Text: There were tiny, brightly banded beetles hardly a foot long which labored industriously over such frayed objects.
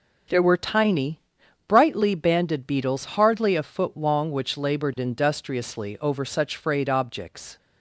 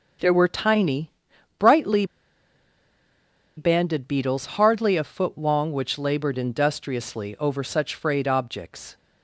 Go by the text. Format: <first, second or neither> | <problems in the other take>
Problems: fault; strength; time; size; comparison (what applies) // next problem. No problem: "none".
first | pauses between "brightly" and "banded"; strong; at 2.0 s; 1.5 s long